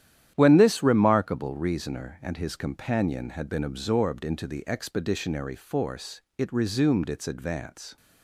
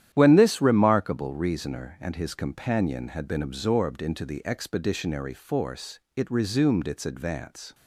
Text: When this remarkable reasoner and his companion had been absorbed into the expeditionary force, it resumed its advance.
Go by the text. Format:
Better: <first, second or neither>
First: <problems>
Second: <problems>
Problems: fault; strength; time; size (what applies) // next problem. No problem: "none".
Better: neither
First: starts louder than the rest; strong; until 1.3 s; 11 dB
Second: starts louder than the rest; strong; until 1.1 s; 11 dB